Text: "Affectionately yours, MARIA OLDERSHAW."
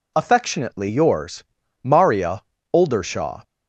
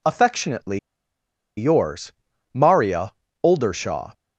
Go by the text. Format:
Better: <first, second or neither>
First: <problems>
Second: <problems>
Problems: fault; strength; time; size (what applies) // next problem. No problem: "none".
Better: first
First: pauses between "MARIA" and "OLDERSHAW"; slight; at 2.4 s; 0.30 s long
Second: pauses between "Affectionately" and "yours"; noticeable; at 0.7 s; 0.79 s long // pauses between "MARIA" and "OLDERSHAW"; slight; at 3.1 s; 0.30 s long